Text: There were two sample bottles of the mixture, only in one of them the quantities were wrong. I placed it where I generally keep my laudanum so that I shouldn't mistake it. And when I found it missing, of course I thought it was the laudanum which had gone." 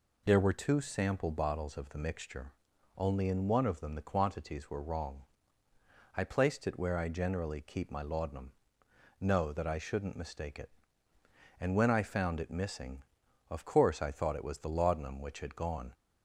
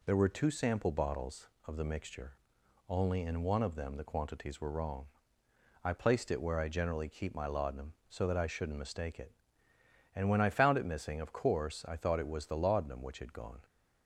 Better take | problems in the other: second | says "no" for "so"; at 9.1 s

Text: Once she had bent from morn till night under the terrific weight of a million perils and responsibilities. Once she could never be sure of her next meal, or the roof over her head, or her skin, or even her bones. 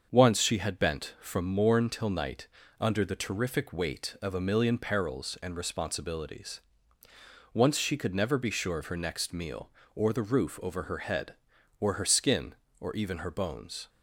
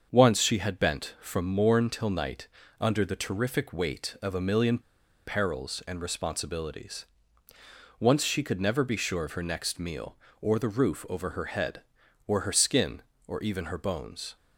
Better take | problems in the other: first | starts louder than the rest; until 1.1 s; 6.5 dB; also in the first // pauses between "night" and "under"; slight; at 2.4 s; 0.32 s long; slight in the first // pauses between "million" and "perils"; noticeable; at 4.7 s; 0.47 s long

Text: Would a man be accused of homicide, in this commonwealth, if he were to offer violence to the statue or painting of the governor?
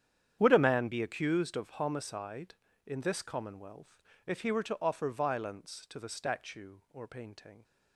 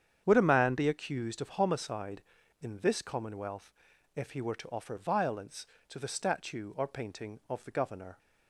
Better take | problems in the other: second | starts louder than the rest; strong; until 1.4 s; 9 dB; strong in the second // stops before "of the governor"; at 7.6 s

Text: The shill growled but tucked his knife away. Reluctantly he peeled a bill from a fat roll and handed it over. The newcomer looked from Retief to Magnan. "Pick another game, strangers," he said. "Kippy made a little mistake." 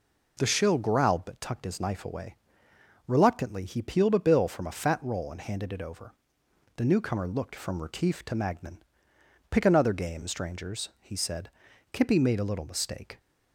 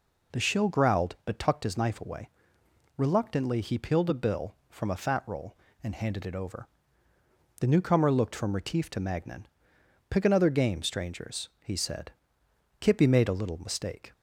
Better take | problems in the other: neither | none

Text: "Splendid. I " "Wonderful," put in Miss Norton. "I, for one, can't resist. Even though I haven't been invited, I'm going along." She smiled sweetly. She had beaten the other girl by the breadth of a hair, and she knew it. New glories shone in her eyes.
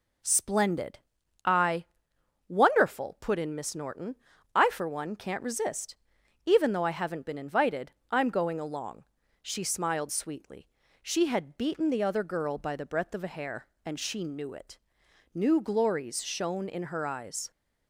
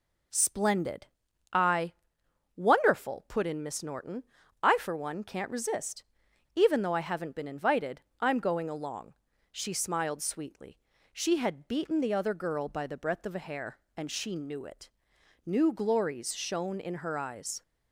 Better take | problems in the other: neither | none

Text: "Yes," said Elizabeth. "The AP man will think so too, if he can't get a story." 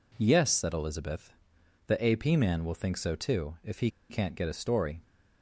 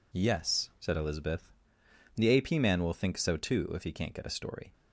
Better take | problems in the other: second | pauses between "he" and "can't"; slight; at 3.8 s; 0.20 s long

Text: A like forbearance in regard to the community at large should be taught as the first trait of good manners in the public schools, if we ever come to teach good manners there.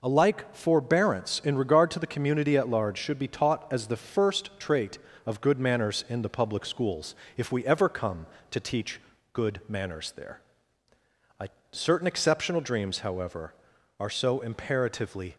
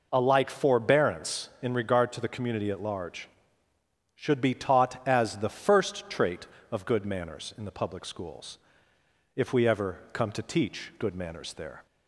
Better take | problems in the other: second | pauses between "teach" and "good"; slight; at 9.0 s; 0.32 s long // goes on to say "I Certain exceptional dreams however are so imperatively"; strong; from 11.3 s on; 3.9 s long

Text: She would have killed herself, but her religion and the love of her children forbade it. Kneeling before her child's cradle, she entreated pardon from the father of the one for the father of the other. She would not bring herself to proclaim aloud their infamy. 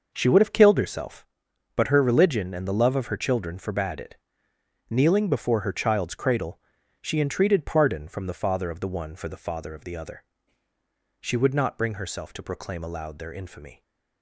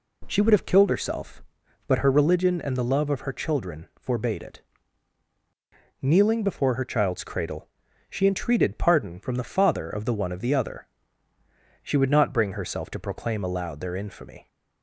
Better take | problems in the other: first | skips "for the father"; at 10.3 s

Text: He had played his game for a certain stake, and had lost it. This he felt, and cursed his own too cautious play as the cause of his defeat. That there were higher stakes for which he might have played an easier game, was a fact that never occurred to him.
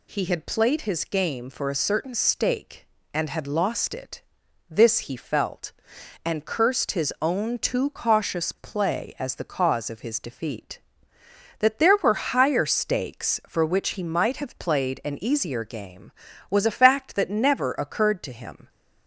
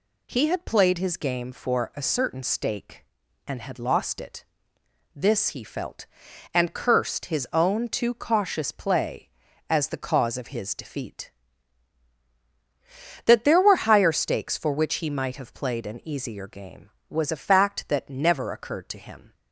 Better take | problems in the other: neither | none

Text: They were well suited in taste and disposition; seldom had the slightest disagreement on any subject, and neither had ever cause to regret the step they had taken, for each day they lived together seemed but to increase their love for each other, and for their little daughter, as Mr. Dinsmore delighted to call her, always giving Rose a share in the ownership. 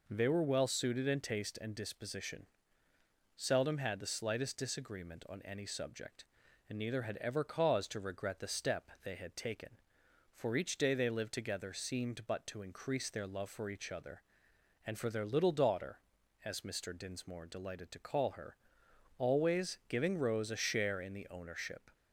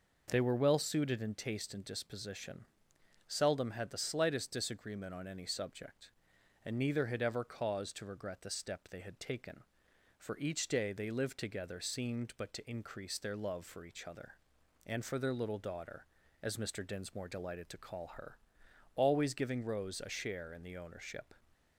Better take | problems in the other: neither | none

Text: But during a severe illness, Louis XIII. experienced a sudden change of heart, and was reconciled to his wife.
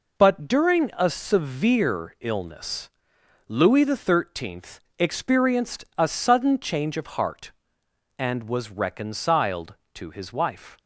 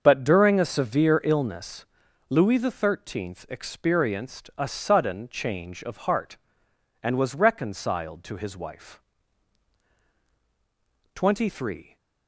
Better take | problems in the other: first | starts louder than the rest; until 1.0 s; 6.5 dB // goes on to say "Twenty three"; noticeable; from 11.1 s on; 0.82 s long

